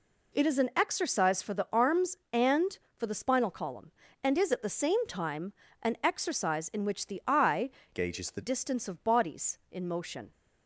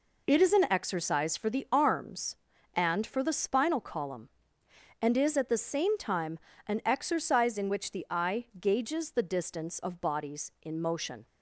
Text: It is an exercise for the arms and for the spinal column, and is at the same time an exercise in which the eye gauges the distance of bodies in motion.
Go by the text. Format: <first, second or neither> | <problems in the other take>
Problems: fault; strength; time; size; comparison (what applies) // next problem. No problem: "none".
second | pauses between "time" and "an"; slight; at 5.5 s; 0.30 s long; slight in the second // changes voice from "gauges" to "the"; from 7.9 to 8.4 s; 0.5 s long